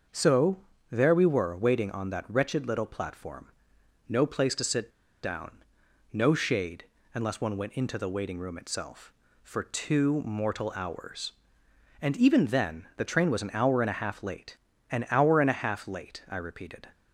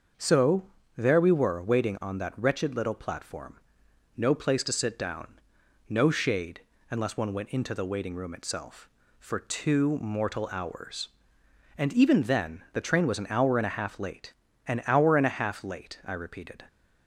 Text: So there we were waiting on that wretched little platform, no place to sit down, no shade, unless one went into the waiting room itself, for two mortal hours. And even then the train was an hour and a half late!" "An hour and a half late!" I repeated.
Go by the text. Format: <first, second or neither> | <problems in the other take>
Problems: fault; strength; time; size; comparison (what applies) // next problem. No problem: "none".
second | starts louder than the rest; until 1.4 s; 6.5 dB; also in the second // pauses between "So" and "there"; slight; at 0.5 s; 0.34 s long; slight in the second // pauses between "sit" and "down"; slight; at 4.8 s; 0.34 s long